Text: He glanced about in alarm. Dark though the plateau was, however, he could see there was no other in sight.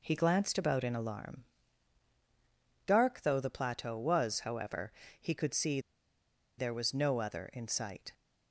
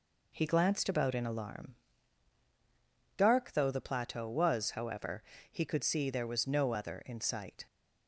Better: second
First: pauses between "see" and "there"; noticeable; at 5.7 s; 0.78 s long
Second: none

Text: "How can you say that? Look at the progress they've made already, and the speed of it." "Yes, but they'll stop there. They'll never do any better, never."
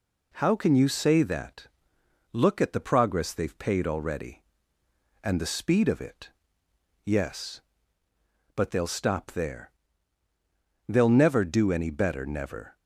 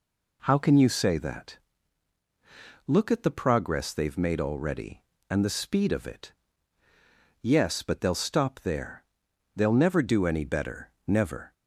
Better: second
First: says "paid" for "made"; at 3.5 s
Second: none

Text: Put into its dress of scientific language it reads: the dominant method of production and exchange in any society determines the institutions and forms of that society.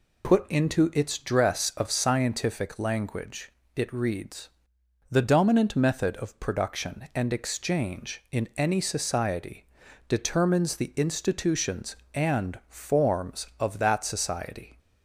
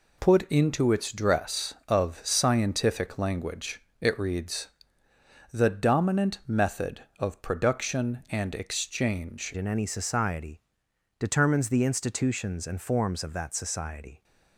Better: first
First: pauses between "language" and "it"; slight; at 3.5 s; 0.24 s long // pauses between "society" and "determines"; at 9.6 s; 0.42 s long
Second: pauses between "language" and "it"; slight; at 3.8 s; 0.20 s long // changes voice at "in"; from 9.5 s on; 4.7 s long // pauses between "society" and "determines"; noticeable; at 10.6 s; 0.58 s long

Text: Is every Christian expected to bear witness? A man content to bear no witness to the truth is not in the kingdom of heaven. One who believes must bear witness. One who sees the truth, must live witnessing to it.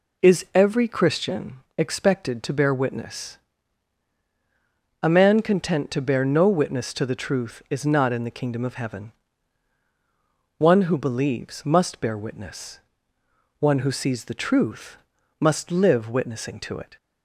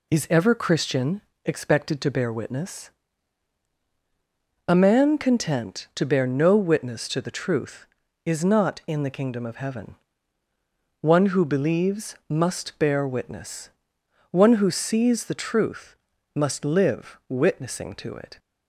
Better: first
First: pauses between "Christian" and "expected"; slight; at 1.5 s; 0.18 s long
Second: says "ever" for "every"; at 0.3 s // pauses between "Christian" and "expected"; slight; at 1.2 s; 0.24 s long

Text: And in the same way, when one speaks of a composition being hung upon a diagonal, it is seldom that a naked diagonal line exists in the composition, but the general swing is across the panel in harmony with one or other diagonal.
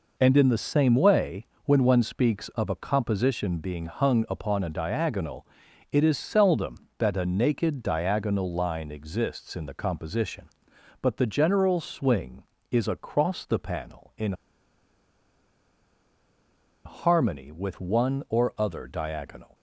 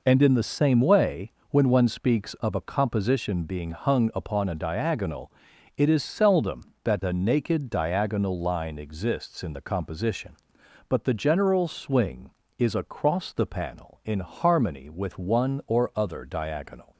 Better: second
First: pauses between "in" and "harmony"; strong; at 14.3 s; 2.5 s long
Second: none

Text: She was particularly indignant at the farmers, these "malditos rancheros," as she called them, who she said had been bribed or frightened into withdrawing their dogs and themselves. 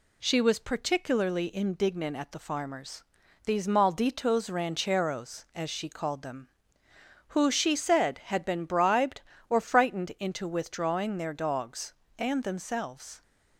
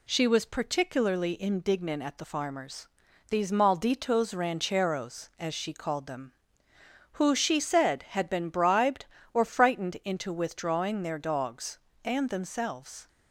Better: neither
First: none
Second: none

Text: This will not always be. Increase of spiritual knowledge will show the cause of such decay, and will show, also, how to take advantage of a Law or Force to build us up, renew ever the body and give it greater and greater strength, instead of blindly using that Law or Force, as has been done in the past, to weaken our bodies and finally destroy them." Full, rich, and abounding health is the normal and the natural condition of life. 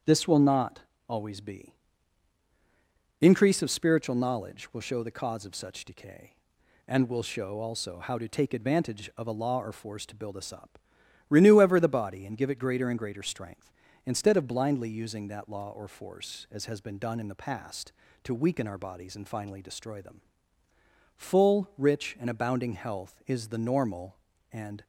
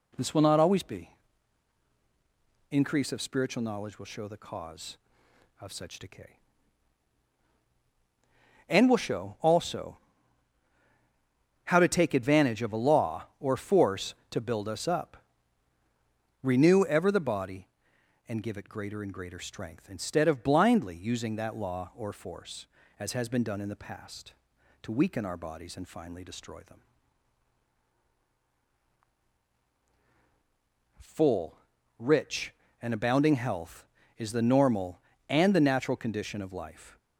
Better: second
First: starts louder than the rest; strong; until 1.3 s; 7.5 dB // pauses between "not" and "always"; slight; at 0.8 s; 0.26 s long // stops before "the natural condition of life"; at 24.8 s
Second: none

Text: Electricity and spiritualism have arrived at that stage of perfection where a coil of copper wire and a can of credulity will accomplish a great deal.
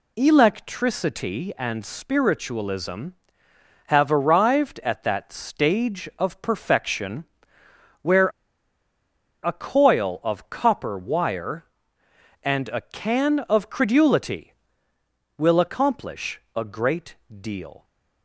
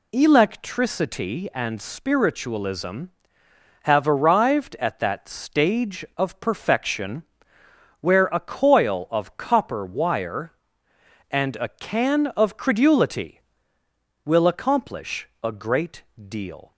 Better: second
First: pauses between "perfection" and "where"; noticeable; at 7.2 s; 0.78 s long // pauses between "where" and "a"; at 8.2 s; 1.1 s long // pauses between "accomplish" and "a"; slight; at 16.3 s; 0.16 s long // pauses between "great" and "deal"; slight; at 17.1 s; 0.26 s long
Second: pauses between "perfection" and "where"; noticeable; at 7.2 s; 0.78 s long // pauses between "accomplish" and "a"; slight; at 15.2 s; 0.16 s long // pauses between "great" and "deal"; slight; at 16.0 s; 0.26 s long

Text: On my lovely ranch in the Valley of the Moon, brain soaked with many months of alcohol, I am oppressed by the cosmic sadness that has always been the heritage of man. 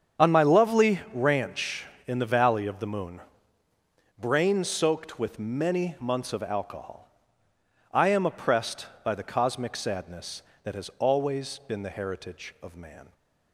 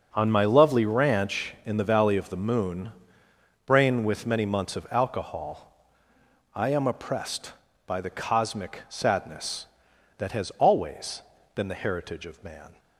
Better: first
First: starts louder than the rest; strong; until 1.3 s; 8 dB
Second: starts louder than the rest; strong; until 1.1 s; 7.5 dB // skips "soaked"; at 4.0 s // pauses between "always" and "been"; slight; at 11.2 s; 0.32 s long

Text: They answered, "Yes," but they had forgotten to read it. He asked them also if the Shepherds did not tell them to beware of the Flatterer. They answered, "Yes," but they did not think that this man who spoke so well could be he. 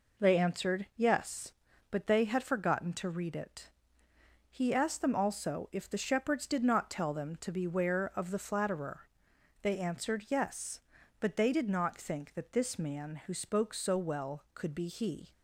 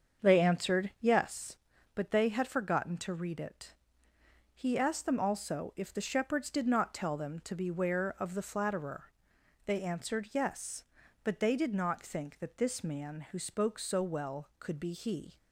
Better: first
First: none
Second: starts louder than the rest; strong; until 1.2 s; 7 dB

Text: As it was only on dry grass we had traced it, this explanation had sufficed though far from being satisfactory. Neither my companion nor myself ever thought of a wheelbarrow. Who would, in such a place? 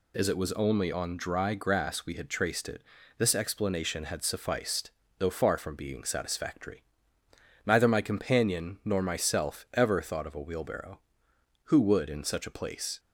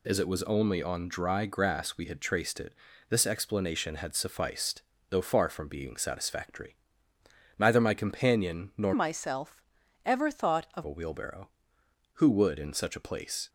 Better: first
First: pauses between "sufficed" and "though"; slight; at 4.9 s; 0.28 s long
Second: pauses between "sufficed" and "though"; slight; at 4.8 s; 0.28 s long // changes voice from "myself" to "of"; from 8.9 to 10.8 s; 1.9 s long // pauses between "myself" and "ever"; at 9.6 s; 0.44 s long

